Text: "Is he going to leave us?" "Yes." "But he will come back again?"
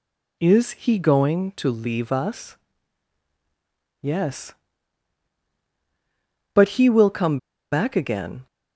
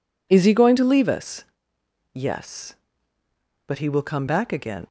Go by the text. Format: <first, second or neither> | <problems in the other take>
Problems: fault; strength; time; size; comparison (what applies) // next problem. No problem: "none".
second | pauses between "come" and "back"; slight; at 7.3 s; 0.33 s long